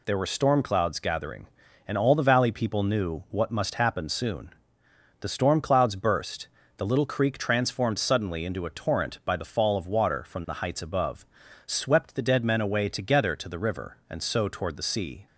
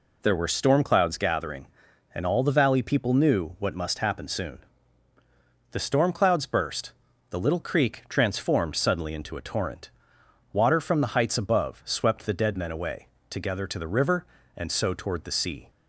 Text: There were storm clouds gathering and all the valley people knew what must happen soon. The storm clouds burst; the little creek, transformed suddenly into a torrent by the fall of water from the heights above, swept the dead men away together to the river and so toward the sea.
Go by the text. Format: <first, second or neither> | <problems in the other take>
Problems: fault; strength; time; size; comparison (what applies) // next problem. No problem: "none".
first | skips "by the fall of"; at 10.2 s // pauses between "away" and "together"; slight; at 13.0 s; 0.24 s long